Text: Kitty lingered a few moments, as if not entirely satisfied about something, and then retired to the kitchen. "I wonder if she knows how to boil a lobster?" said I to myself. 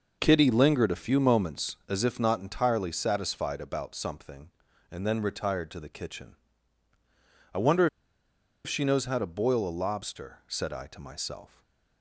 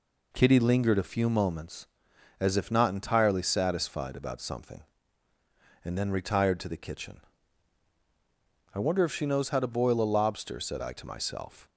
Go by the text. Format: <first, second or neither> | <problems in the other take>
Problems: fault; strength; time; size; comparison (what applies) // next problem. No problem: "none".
second | pauses between "wonder" and "if"; noticeable; at 7.8 s; 0.78 s long // stays silent after the last word; slight; from 11.4 s on; 0.6 s long